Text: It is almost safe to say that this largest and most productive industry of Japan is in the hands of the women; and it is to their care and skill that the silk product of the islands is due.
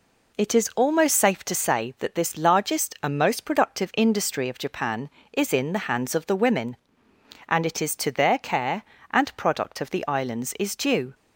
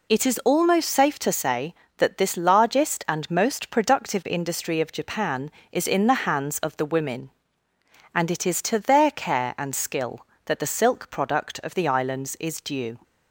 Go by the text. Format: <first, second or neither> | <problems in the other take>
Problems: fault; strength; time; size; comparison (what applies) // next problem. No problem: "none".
second | skips "skill that the silk"; at 9.3 s